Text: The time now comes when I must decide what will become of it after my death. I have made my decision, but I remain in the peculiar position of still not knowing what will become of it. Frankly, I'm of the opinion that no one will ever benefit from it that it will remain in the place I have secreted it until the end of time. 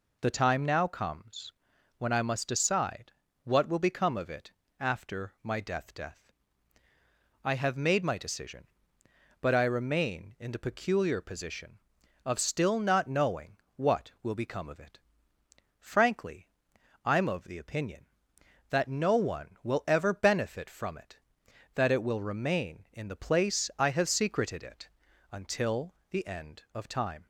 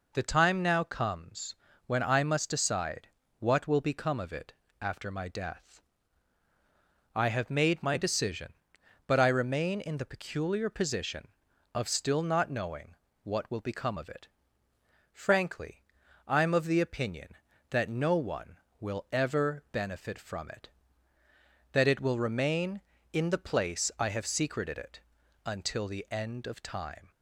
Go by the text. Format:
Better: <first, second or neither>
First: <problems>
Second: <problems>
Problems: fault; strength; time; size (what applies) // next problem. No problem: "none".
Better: second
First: pauses between "comes" and "when"; noticeable; at 1.5 s; 0.46 s long // pauses between "decide" and "what"; slight; at 3.1 s; 0.32 s long // pauses between "it" and "after"; slight; at 4.5 s; 0.26 s long // says "death" twice; at 5.9 s // pauses between "knowing" and "what"; slight; at 13.5 s; 0.18 s long // pauses between "it" and "until"; at 24.8 s; 0.42 s long // pauses between "until" and "the"; slight; at 25.9 s; 0.16 s long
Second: pauses between "comes" and "when"; slight; at 1.5 s; 0.32 s long // pauses between "decide" and "what"; slight; at 3.0 s; 0.32 s long // pauses between "it" and "after"; slight; at 4.5 s; 0.28 s long // pauses between "knowing" and "what"; slight; at 12.9 s; 0.28 s long // pauses between "it" and "until"; at 25.0 s; 0.44 s long